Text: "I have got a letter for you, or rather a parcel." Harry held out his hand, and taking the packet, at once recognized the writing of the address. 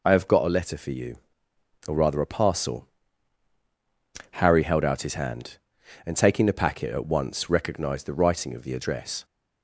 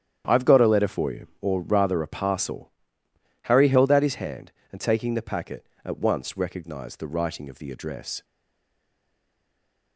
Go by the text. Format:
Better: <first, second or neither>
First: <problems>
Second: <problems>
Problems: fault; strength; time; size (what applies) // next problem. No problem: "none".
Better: first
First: none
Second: starts louder than the rest; strong; until 1.2 s; 9.5 dB // stays silent after the last word; noticeable; from 8.2 s on; 1.7 s long